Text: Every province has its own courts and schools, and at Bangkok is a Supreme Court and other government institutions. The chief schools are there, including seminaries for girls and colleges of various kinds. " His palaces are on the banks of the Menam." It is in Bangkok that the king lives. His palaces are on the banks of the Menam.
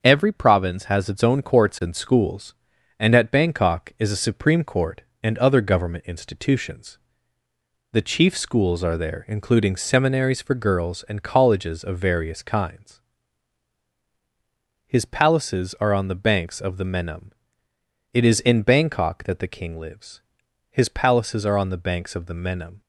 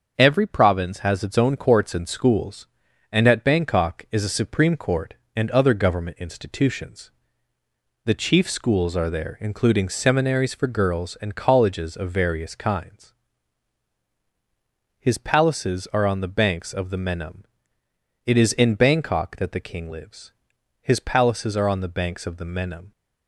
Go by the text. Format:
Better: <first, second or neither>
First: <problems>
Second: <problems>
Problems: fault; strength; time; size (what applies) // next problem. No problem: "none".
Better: neither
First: starts louder than the rest; until 1.0 s; 6.5 dB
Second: starts louder than the rest; until 1.1 s; 6.5 dB